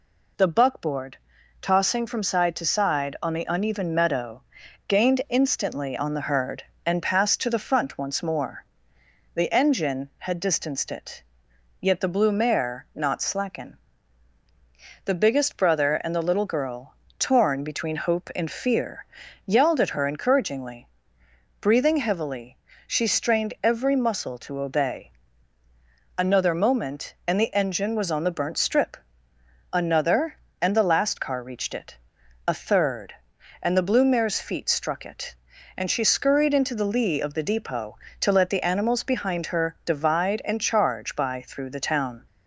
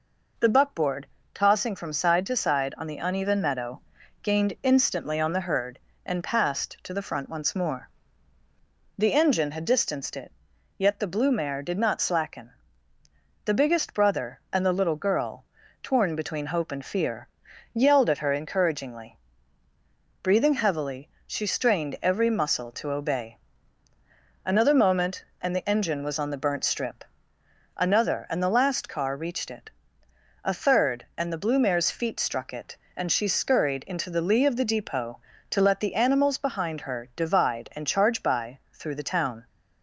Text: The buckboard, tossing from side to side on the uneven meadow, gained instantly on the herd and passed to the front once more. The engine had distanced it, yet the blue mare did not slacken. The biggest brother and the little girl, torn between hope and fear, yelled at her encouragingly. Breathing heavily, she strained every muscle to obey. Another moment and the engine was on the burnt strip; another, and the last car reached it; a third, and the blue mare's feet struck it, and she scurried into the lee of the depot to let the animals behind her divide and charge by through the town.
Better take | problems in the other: second | skips "did"; at 12.8 s

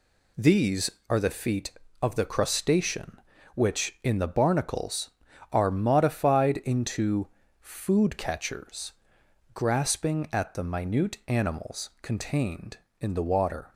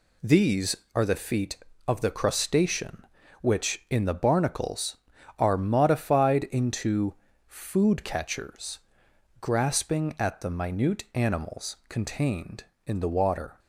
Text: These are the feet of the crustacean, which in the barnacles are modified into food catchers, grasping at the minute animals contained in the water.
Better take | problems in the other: neither | pauses between "into" and "food"; slight; the same in both

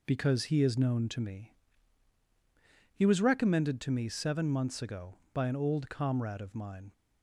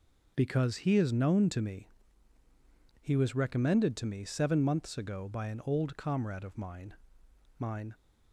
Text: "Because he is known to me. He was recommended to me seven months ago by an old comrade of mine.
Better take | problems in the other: first | says "mine" twice; at 7.6 s

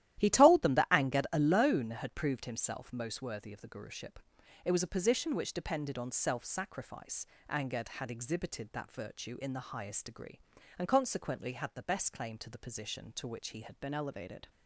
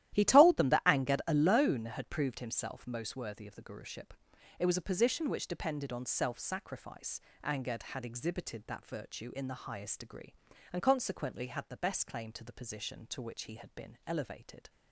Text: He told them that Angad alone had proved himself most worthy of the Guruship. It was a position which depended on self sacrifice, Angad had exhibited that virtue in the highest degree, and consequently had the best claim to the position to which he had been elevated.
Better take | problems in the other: second | starts louder than the rest; strong; until 1.2 s; 13 dB; strong in the second // changes voice at "been"; from 13.8 s on; 0.6 s long

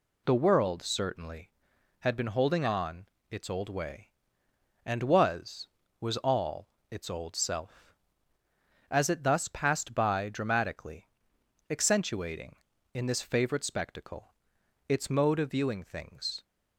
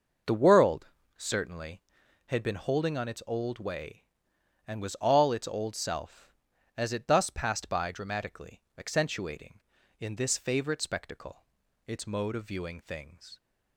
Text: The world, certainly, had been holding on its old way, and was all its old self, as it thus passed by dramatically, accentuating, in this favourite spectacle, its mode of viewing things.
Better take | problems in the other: second | pauses between "on" and "its"; slight; at 3.0 s; 0.24 s long // says "was" twice; at 5.9 s // pauses between "all" and "its"; slight; at 6.6 s; 0.22 s long

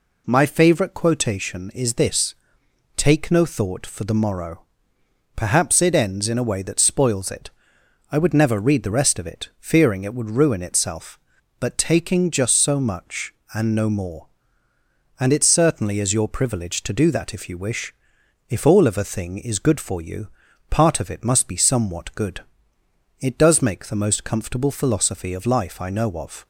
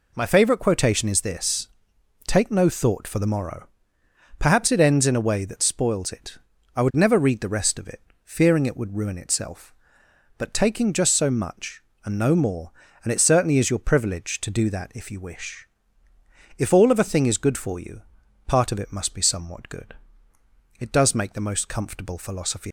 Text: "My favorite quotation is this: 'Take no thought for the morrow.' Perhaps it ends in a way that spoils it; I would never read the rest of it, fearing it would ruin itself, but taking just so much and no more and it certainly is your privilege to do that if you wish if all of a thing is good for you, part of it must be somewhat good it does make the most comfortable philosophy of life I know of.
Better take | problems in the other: first | pauses between "wish" and "if"; noticeable; at 15.6 s; 0.90 s long; noticeable in the first // pauses between "good" and "it"; noticeable; at 19.9 s; 0.84 s long; noticeable in the first // stops before "of life I know of"; at 22.6 s

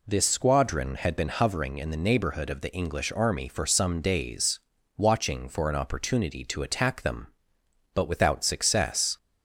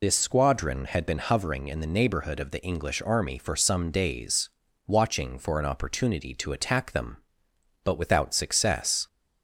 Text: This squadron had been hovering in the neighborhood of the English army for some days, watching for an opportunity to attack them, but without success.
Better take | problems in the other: first | loses the start of "This"; at 0.0 s; 75 ms

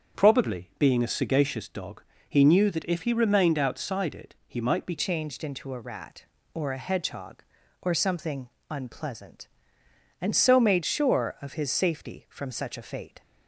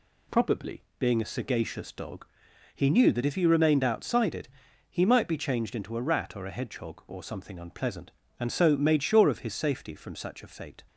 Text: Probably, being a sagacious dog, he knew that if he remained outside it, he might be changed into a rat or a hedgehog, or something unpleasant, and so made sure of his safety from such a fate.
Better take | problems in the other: second | starts louder than the rest; strong; until 1.2 s; 7 dB // changes voice at "changed"; from 4.9 s on; 8.3 s long // pauses between "something" and "unpleasant"; slight; at 8.4 s; 0.22 s long

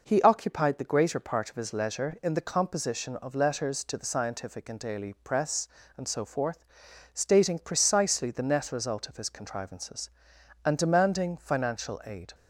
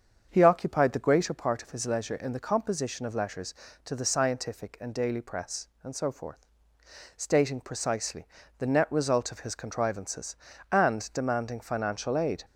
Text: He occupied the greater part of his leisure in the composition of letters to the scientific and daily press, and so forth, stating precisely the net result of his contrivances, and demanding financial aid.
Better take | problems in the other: first | starts louder than the rest; strong; until 1.3 s; 7.5 dB // pauses between "precisely" and "the"; slight; at 8.2 s; 0.32 s long

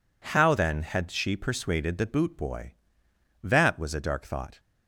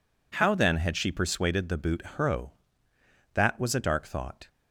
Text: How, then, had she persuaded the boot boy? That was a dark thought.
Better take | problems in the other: first | says "hro" for "boy"; at 2.1 s

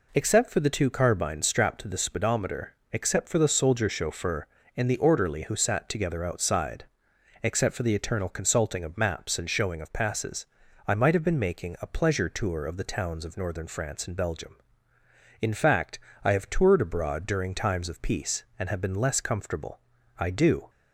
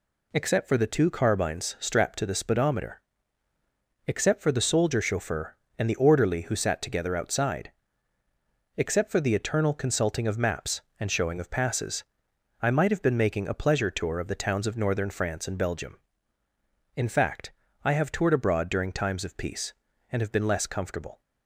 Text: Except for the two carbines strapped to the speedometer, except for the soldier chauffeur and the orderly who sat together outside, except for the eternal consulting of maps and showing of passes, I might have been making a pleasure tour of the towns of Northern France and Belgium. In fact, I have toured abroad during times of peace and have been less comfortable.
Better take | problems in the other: second | goes on to say "I do"; from 20.1 s on; 0.52 s long

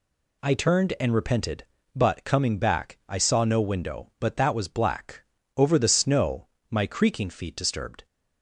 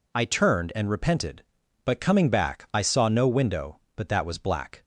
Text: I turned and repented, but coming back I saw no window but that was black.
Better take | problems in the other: second | goes on to say "Over the snow my creaking feet Disturbed"; strong; from 5.5 s on; 2.4 s long

